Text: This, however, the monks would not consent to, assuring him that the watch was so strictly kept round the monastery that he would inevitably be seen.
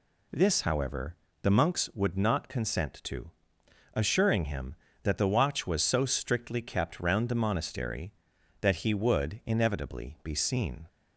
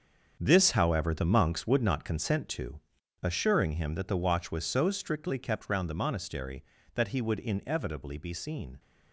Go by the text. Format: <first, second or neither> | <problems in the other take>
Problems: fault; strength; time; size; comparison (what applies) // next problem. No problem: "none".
first | gets quieter; strong; throughout; 11 dB